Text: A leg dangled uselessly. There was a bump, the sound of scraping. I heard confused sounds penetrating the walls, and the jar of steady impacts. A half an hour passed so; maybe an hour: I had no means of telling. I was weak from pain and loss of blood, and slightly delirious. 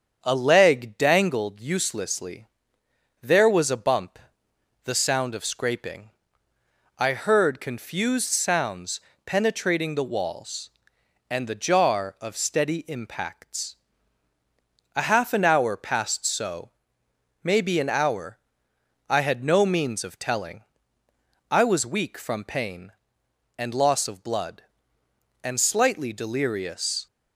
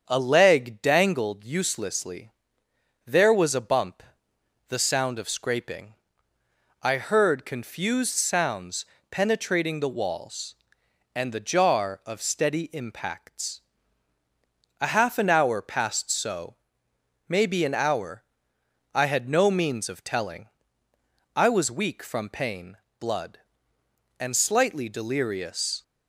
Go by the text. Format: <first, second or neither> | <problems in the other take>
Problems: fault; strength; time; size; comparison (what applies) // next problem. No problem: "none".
first | starts louder than the rest; strong; until 1.0 s; 7 dB; strong in the first // pauses between "sounds" and "penetrating"; slight; at 8.8 s; 0.24 s long; slight in the first // skips "and loss of"; at 22.8 s